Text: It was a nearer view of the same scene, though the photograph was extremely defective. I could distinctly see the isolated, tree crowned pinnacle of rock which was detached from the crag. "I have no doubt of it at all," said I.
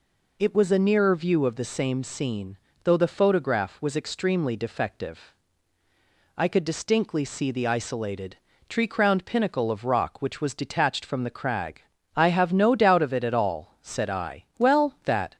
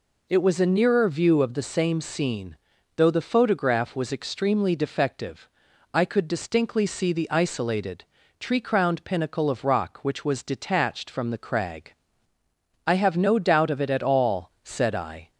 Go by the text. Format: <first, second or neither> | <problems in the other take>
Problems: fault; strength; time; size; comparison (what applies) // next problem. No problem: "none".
second | goes on to say "Well that"; noticeable; from 14.5 s on; 0.78 s long